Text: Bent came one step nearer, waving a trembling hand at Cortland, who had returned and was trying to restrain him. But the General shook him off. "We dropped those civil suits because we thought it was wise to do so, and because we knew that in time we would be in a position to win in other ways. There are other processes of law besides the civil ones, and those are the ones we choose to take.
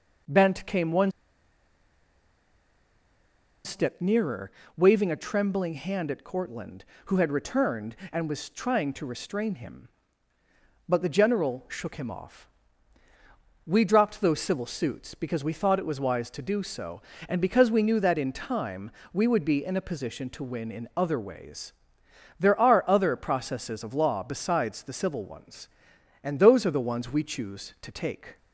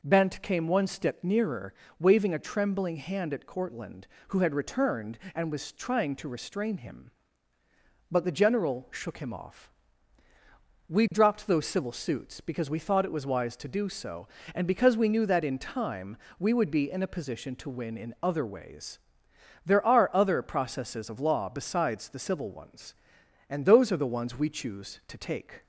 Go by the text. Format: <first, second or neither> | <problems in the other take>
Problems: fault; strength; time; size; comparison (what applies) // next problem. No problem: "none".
second | pauses between "one" and "step"; strong; at 1.1 s; 2.5 s long // pauses between "time" and "we"; slight; at 18.9 s; 0.20 s long; slight in the second